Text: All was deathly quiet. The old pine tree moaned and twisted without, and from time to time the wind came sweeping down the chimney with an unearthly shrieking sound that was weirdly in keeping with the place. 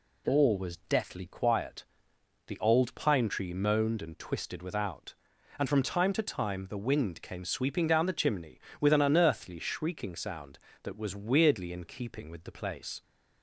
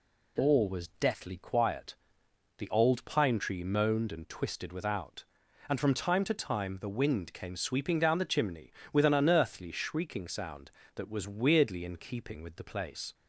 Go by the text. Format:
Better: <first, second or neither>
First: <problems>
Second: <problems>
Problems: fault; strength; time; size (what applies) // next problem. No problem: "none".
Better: neither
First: none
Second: none